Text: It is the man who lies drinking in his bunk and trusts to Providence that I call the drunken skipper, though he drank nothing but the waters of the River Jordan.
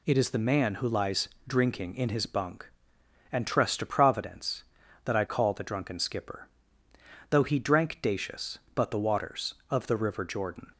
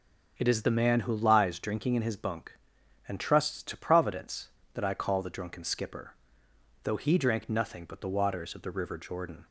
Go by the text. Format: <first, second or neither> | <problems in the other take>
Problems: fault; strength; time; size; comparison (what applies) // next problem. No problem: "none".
second | pauses between "lies" and "drinking"; slight; at 1.2 s; 0.20 s long // says "dacious" for "nothing"; at 8.0 s